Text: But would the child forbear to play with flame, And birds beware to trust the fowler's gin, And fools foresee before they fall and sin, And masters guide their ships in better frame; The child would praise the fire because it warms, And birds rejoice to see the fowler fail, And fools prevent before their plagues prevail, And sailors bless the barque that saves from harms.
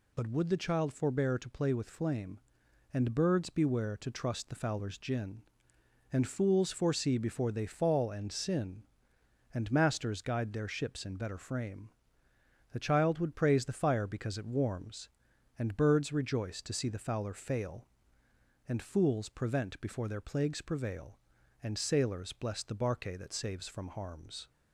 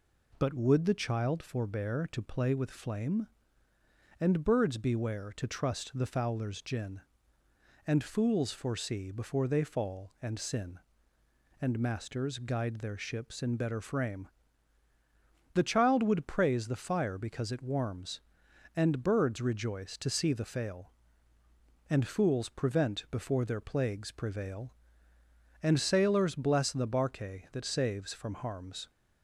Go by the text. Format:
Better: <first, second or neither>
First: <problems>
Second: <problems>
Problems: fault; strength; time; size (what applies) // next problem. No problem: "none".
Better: first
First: none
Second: skips "fowler"; at 20.4 s